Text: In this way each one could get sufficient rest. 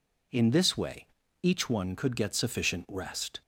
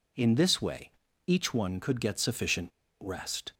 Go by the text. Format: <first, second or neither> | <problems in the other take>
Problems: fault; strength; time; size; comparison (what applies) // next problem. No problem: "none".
first | pauses between "way" and "each"; slight; at 0.8 s; 0.36 s long; slight in the first // pauses between "sufficient" and "rest"; slight; at 2.6 s; 0.32 s long